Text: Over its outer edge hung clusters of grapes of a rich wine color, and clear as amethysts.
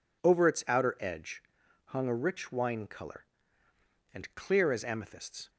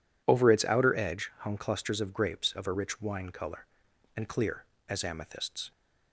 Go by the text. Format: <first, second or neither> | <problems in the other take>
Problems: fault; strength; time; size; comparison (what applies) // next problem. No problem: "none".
second | pauses between "edge" and "hung"; at 1.4 s; 0.44 s long // skips "clusters of grapes of"; at 2.0 s